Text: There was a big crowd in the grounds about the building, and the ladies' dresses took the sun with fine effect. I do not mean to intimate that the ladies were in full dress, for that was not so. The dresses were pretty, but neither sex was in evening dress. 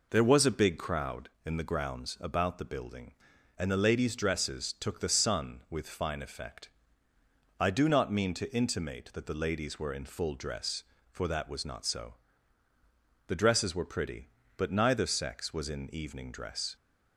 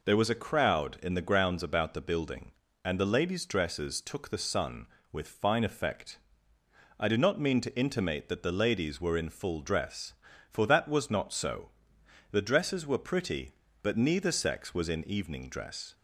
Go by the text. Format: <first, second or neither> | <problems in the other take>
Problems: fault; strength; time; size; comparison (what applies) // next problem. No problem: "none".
first | skips "big"; at 0.4 s